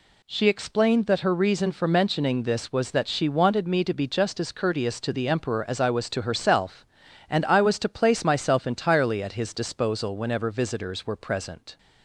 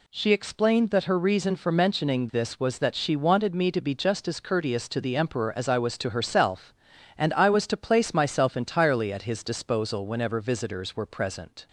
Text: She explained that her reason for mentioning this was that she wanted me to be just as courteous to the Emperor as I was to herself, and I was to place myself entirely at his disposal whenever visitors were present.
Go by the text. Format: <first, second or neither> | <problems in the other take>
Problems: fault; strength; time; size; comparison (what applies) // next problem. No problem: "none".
neither | none